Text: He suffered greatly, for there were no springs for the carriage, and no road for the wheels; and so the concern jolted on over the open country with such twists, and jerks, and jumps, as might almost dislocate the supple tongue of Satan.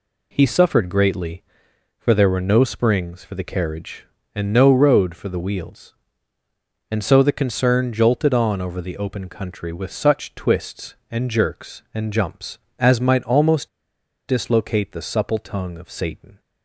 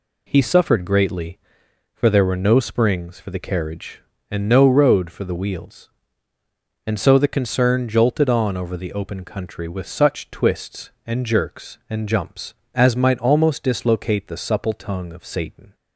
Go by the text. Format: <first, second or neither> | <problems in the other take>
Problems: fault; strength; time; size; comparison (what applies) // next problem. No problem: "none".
second | pauses between "almost" and "dislocate"; noticeable; at 13.6 s; 0.60 s long